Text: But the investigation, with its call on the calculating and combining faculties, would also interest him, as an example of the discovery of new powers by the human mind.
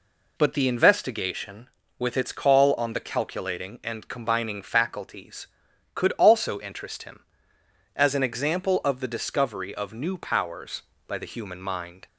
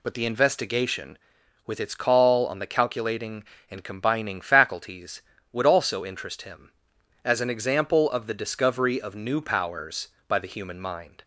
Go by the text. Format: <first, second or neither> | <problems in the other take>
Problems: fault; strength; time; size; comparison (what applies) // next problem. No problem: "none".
second | says "could" for "would"; at 5.9 s